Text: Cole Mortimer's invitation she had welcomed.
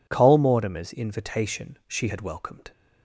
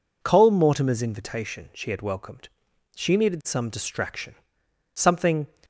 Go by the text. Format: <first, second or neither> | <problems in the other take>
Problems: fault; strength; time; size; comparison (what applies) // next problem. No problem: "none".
first | goes on to say "She needed some distraction something"; strong; from 2.9 s on; 2.5 s long